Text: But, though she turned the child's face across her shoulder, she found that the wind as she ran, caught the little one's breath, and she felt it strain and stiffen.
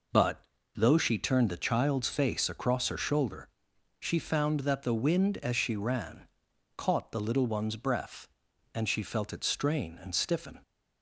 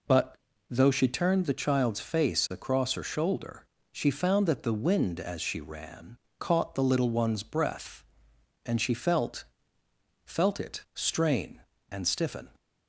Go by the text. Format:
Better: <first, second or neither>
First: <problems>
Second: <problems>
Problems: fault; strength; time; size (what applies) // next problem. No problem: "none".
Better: first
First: none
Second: says "felt" twice; at 10.2 s